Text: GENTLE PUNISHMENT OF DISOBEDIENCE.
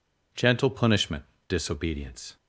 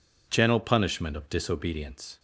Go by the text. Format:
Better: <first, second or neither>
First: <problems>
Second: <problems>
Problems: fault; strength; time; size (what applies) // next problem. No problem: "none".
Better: second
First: skips "OF"; at 1.3 s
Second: none